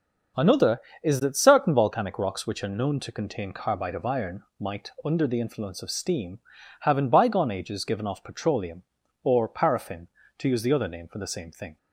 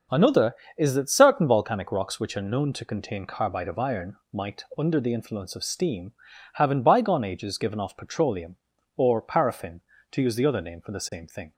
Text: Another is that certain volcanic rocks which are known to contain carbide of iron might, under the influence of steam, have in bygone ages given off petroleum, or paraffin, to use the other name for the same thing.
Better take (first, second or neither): neither